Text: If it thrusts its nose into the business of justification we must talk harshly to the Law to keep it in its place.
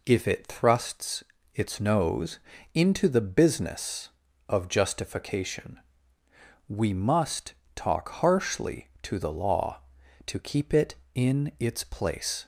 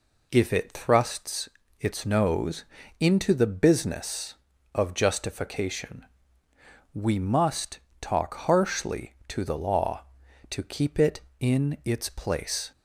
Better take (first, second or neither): neither